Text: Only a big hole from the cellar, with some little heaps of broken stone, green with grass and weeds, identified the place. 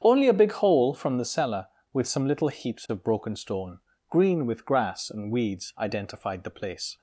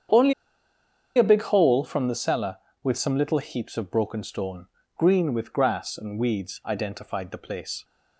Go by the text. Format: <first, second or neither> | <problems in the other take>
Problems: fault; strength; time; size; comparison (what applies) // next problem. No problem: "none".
first | starts louder than the rest; strong; until 1.9 s; 8 dB; strong in the first // pauses between "Only" and "a"; noticeable; at 0.3 s; 0.83 s long